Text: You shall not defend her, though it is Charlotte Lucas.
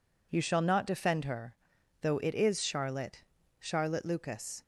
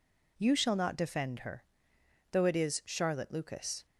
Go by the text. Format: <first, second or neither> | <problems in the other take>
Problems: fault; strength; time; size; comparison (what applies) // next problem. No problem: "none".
second | says "Charlotte" twice; at 3.5 s